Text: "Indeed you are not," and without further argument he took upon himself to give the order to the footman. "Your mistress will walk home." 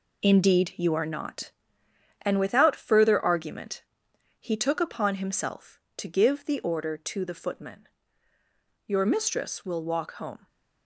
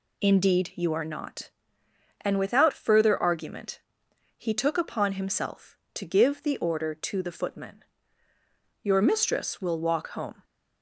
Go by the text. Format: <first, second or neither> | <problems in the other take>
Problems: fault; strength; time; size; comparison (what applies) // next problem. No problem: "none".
second | gets quieter; strong; throughout; 8 dB // pauses between "argument" and "he"; noticeable; at 3.8 s; 0.56 s long; noticeable in the second